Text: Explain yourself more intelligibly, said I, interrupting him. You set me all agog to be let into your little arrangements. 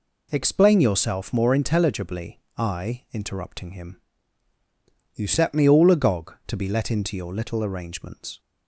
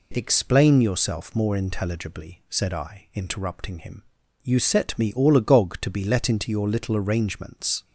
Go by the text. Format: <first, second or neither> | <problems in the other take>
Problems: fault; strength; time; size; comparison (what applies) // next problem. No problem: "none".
second | skips "said"; at 2.4 s